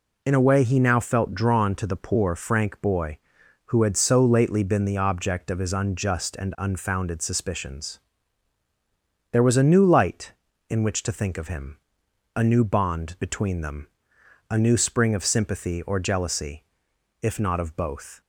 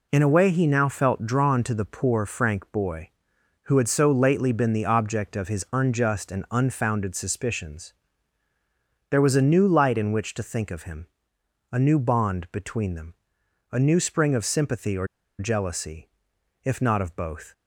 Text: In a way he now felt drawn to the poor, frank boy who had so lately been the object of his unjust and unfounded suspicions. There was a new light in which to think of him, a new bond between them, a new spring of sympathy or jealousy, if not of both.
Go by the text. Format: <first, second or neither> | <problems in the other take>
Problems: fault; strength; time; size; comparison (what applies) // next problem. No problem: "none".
first | pauses between "or" and "jealousy"; slight; at 15.0 s; 0.32 s long